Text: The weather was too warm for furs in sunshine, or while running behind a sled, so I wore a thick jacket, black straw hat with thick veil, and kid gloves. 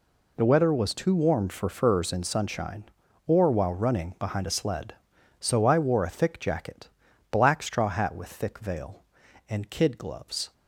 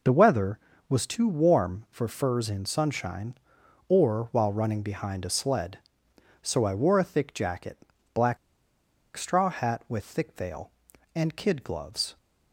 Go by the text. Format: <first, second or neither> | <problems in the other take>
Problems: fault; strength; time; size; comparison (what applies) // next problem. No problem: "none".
first | pauses between "black" and "straw"; noticeable; at 8.3 s; 0.79 s long